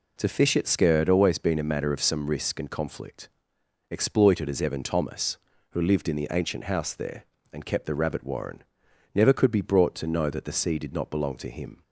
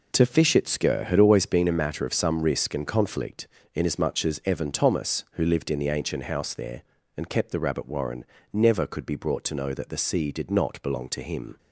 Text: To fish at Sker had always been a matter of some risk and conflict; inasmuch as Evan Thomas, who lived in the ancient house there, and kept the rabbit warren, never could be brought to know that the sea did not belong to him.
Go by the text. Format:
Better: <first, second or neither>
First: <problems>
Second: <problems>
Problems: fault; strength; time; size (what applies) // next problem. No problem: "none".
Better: second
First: says "exploited" for "inasmuch"; at 3.9 s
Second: none